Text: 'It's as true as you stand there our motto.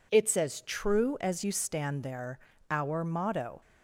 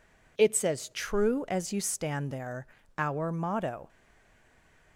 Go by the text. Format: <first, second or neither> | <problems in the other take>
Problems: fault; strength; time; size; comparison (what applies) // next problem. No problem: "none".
first | pauses between "there" and "our"; slight; at 2.6 s; 0.32 s long; slight in the first // stays silent after the last word; from 3.8 s on; 1.1 s long